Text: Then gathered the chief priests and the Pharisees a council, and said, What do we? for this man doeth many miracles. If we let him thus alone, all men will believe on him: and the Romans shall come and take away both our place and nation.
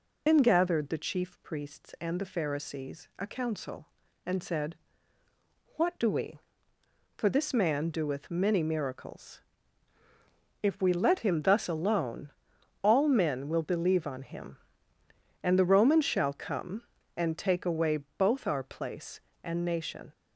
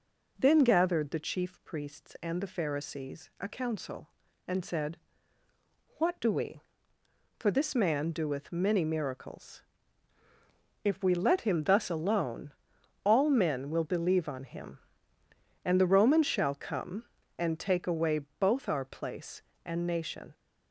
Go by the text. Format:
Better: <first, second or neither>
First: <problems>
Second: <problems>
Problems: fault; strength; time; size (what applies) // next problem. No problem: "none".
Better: second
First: loses the start of "Then"; at 0.2 s; 110 ms // pauses between "away" and "both"; slight; at 17.9 s; 0.20 s long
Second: pauses between "away" and "both"; slight; at 18.1 s; 0.20 s long